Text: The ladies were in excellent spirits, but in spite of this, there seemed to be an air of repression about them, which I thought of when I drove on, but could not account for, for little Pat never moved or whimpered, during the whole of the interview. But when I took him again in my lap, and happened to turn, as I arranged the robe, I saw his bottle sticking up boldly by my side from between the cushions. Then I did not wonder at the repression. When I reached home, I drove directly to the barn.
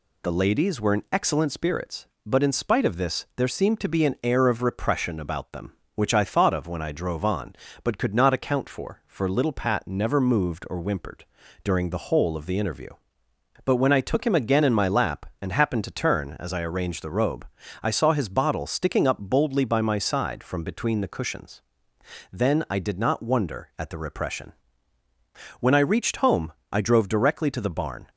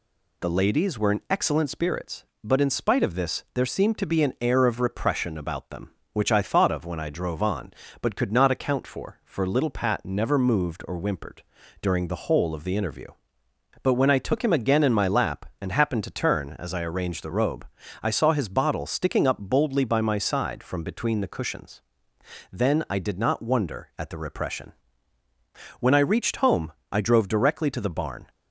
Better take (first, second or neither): neither